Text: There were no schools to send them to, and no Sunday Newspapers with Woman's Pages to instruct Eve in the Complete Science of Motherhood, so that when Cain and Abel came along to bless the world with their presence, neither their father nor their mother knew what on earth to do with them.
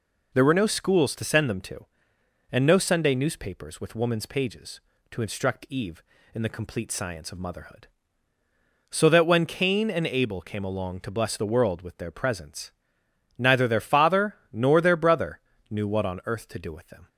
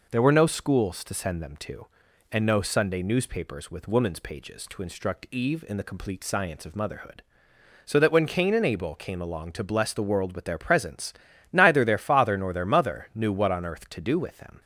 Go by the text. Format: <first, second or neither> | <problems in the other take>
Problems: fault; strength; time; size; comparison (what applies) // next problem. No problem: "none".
second | pauses between "father" and "nor"; slight; at 14.3 s; 0.18 s long // says "brother" for "mother"; at 14.9 s